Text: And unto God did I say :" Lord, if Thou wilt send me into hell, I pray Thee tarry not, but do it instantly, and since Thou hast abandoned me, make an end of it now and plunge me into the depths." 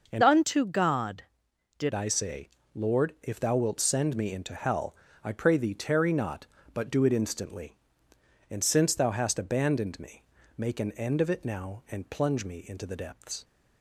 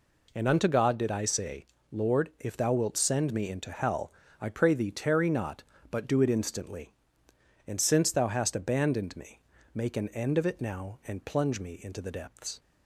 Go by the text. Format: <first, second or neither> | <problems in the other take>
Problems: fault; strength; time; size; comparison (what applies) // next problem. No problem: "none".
second | starts louder than the rest; noticeable; until 1.1 s; 6 dB // changes voice from "unto" to "did"; from 0.2 to 1.9 s; 1.7 s long